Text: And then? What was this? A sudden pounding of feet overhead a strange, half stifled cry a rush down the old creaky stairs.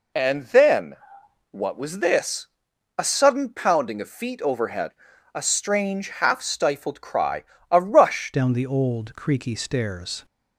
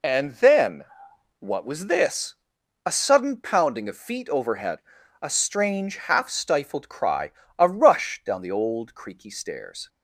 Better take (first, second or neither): second